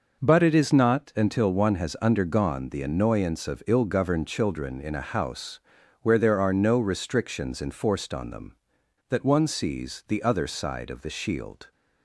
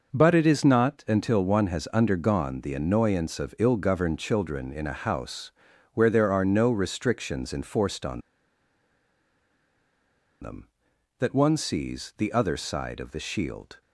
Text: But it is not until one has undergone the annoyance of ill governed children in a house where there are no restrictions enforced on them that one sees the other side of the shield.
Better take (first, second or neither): first